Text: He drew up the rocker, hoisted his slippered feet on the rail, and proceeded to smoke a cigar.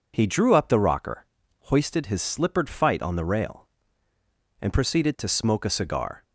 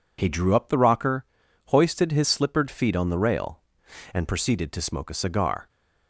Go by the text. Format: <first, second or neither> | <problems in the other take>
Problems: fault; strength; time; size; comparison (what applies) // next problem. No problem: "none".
second | says "fight" for "feet"; at 2.6 s